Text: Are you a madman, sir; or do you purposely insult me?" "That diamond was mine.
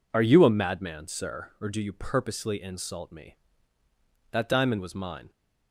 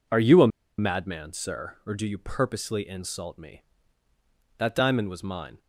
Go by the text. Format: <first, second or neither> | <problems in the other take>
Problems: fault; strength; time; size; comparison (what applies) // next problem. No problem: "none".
first | pauses between "a" and "madman"; slight; at 0.4 s; 0.30 s long